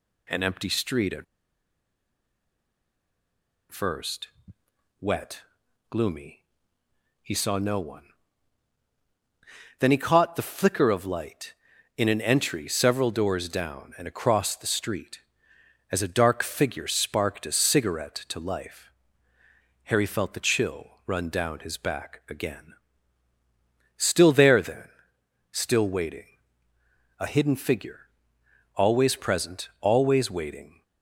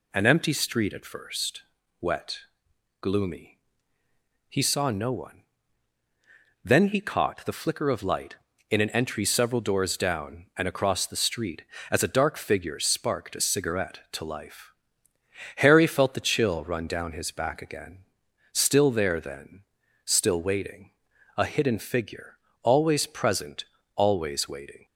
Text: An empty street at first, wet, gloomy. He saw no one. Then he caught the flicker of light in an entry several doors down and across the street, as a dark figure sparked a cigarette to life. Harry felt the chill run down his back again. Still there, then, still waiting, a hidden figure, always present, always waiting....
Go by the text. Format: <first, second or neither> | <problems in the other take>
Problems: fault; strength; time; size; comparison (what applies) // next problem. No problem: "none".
second | pauses between "at" and "first"; strong; at 1.2 s; 2.4 s long